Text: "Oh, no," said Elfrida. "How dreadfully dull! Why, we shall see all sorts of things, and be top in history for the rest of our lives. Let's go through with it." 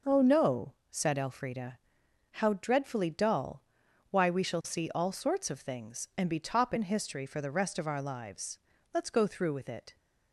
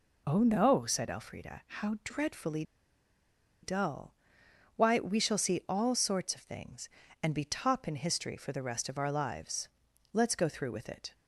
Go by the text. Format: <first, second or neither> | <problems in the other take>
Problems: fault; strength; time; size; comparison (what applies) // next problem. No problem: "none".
first | pauses between "dreadfully" and "dull"; at 2.6 s; 0.99 s long